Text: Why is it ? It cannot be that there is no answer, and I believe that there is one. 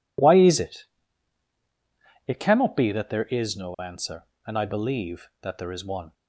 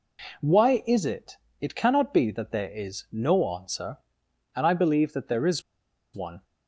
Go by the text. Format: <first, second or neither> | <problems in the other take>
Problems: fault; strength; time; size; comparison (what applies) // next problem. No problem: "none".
first | pauses between "is" and "one"; noticeable; at 5.6 s; 0.52 s long